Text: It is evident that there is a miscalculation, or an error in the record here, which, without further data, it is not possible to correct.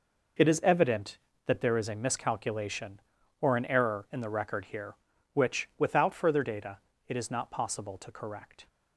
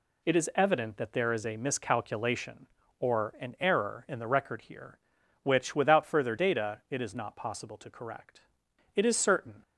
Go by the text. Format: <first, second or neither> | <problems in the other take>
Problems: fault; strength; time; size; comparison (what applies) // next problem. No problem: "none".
first | goes on to say "It is certain"; noticeable; from 8.9 s on; 0.66 s long